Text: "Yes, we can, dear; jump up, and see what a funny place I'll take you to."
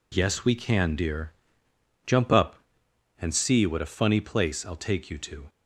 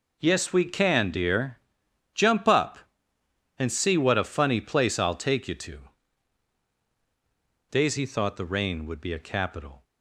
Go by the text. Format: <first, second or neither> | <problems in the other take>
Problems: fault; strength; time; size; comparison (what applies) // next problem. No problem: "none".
first | goes on to say "Daisy thought the rain would be a capital"; strong; from 7.6 s on; 2.1 s long